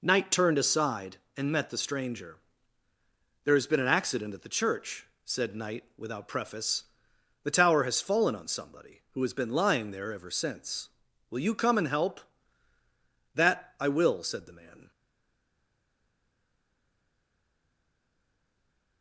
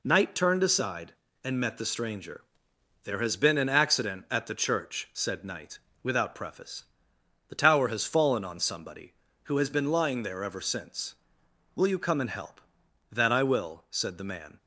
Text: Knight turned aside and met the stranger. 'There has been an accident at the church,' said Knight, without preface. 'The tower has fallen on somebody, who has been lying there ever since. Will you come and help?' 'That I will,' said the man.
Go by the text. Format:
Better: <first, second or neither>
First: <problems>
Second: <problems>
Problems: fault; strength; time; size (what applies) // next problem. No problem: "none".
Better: second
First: stays silent after the last word; strong; from 14.9 s on; 4.1 s long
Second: none